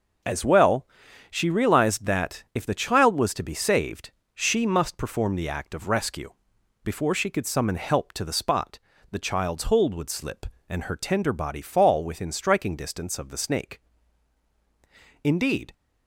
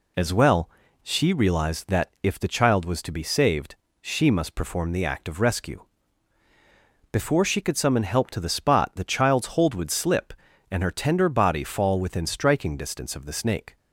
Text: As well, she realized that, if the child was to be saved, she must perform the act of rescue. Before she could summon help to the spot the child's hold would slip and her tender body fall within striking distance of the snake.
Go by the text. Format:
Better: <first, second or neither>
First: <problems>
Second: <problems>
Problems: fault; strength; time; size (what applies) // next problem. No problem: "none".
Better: second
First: pauses between "spot" and "the"; slight; at 8.7 s; 0.32 s long // goes on to say "Indeed"; from 15.2 s on; 0.50 s long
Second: none